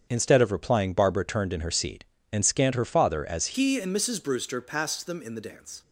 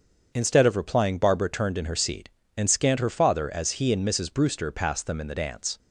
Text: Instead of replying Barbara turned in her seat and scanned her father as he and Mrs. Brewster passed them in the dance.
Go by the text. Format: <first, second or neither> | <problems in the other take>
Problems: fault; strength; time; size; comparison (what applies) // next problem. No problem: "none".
second | starts louder than the rest; strong; until 1.1 s; 7 dB; also in the second // changes voice at "he"; from 3.5 s on; 2.3 s long